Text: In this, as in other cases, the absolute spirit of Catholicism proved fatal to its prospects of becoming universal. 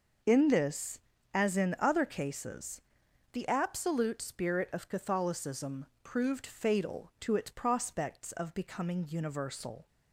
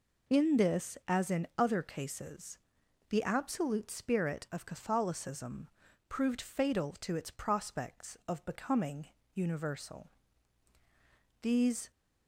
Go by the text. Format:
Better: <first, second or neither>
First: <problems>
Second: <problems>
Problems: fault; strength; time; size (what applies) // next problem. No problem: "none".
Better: first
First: pauses between "Catholicism" and "proved"; slight; at 5.8 s; 0.18 s long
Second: pauses between "Catholicism" and "proved"; at 5.6 s; 0.40 s long // pauses between "becoming" and "universal"; slight; at 9.0 s; 0.26 s long // goes on to say "These"; slight; from 11.4 s on; 0.48 s long